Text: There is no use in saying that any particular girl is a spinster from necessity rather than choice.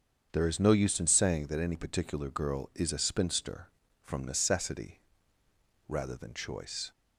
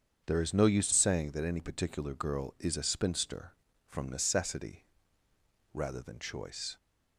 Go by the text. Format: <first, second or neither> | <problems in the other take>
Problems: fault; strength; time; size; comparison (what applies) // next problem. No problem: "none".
first | starts louder than the rest; strong; until 1.2 s; 7 dB; strong in the first // skips "in"; at 0.9 s // pauses between "necessity" and "rather"; noticeable; at 4.8 s; 0.88 s long; noticeable in the first